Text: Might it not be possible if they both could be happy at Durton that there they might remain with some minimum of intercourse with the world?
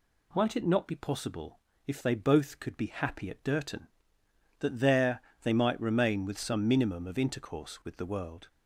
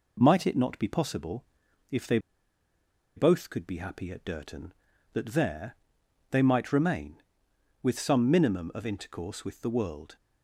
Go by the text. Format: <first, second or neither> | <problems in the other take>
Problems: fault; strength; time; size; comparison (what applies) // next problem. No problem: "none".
first | pauses between "possible" and "if"; noticeable; at 1.4 s; 0.48 s long; slight in the first // pauses between "they" and "both"; at 2.1 s; 0.98 s long // pauses between "there" and "they"; noticeable; at 5.7 s; 0.56 s long; slight in the first